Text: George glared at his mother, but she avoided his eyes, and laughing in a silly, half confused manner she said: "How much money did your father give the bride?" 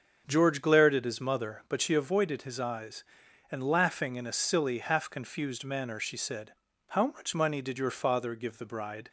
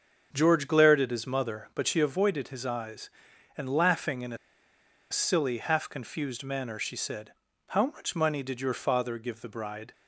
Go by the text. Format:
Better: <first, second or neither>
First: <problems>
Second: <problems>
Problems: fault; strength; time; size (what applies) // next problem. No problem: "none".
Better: first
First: starts louder than the rest; until 1.2 s; 7 dB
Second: starts louder than the rest; until 1.3 s; 7 dB // pauses between "a" and "silly"; noticeable; at 4.3 s; 0.74 s long